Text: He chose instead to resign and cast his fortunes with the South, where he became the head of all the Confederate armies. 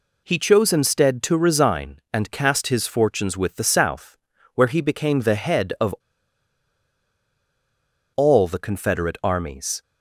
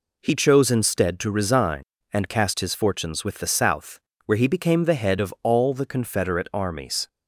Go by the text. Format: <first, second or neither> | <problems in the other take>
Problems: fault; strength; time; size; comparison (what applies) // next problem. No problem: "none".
second | pauses between "of" and "all"; strong; at 5.9 s; 2.2 s long